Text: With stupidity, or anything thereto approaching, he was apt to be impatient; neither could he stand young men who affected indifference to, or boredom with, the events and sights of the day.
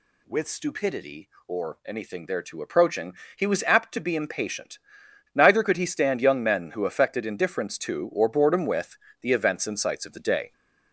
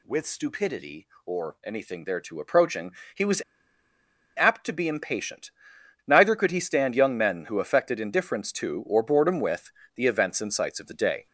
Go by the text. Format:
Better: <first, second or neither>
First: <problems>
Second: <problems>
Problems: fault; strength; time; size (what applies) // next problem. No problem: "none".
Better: first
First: none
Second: pauses between "was" and "apt"; noticeable; at 3.4 s; 0.93 s long